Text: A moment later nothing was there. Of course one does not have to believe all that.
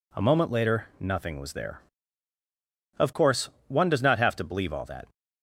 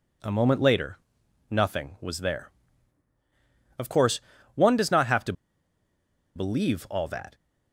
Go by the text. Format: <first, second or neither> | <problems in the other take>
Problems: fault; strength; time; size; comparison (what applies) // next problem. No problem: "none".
first | pauses between "later" and "nothing"; noticeable; at 0.9 s; 0.50 s long // pauses between "course" and "one"; slight; at 4.2 s; 0.34 s long; slight in the first // pauses between "to" and "believe"; at 5.3 s; 1.0 s long